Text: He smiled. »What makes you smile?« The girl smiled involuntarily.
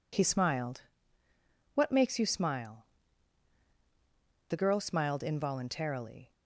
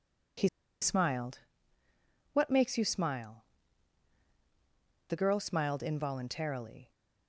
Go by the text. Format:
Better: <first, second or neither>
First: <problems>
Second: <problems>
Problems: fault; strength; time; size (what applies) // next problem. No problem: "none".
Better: first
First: none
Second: pauses between "He" and "smiled"; slight; at 0.4 s; 0.35 s long